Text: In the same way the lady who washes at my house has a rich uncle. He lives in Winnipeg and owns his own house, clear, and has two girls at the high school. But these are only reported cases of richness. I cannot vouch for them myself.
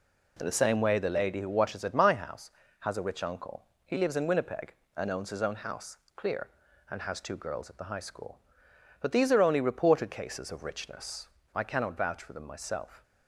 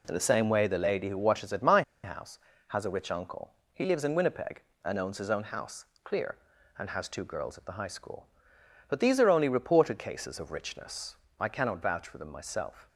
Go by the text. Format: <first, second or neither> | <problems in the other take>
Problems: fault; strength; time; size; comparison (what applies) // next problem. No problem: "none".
first | pauses between "my" and "house"; slight; at 1.8 s; 0.21 s long